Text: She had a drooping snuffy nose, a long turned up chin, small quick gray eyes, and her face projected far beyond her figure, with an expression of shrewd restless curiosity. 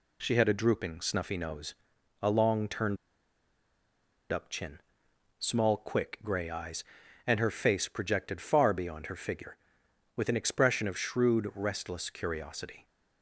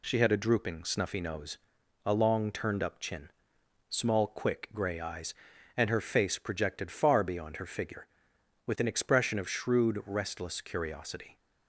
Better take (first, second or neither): second